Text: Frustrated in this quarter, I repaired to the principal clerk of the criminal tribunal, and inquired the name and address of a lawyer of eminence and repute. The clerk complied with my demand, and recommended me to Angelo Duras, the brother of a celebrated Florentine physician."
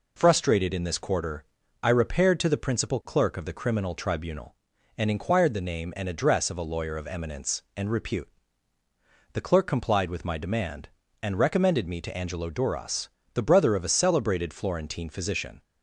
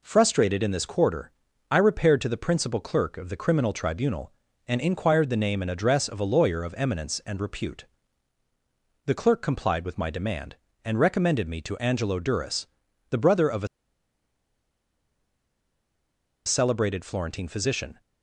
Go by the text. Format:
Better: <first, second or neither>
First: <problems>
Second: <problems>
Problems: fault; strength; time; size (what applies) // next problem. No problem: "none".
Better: first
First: none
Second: pauses between "a" and "celebrated"; strong; at 13.6 s; 2.7 s long